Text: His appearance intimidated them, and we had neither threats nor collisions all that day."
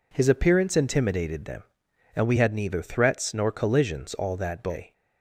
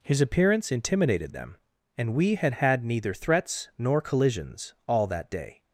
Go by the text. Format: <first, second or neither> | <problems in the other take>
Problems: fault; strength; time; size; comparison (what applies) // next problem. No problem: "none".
first | says "had" twice; at 2.5 s